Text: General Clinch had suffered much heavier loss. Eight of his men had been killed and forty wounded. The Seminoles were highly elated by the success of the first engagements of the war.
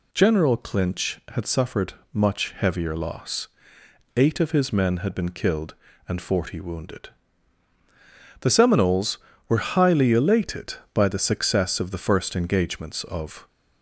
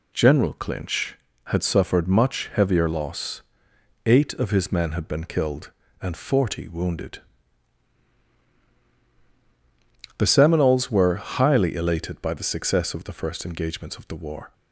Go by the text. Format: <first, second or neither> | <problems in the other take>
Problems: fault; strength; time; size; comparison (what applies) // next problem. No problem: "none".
second | pauses between "suffered" and "much"; slight; at 1.9 s; 0.20 s long // stops before "the war"; at 13.4 s